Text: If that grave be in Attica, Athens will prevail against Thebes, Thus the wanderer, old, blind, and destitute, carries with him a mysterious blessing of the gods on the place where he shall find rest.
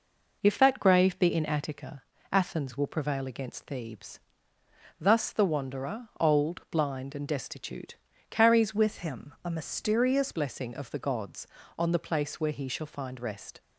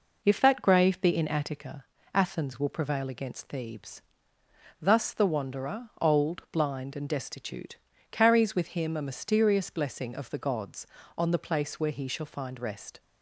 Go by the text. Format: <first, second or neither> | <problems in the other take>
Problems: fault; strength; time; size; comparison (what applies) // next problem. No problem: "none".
second | changes voice from "with" to "mysterious"; from 8.7 to 10.3 s; 1.6 s long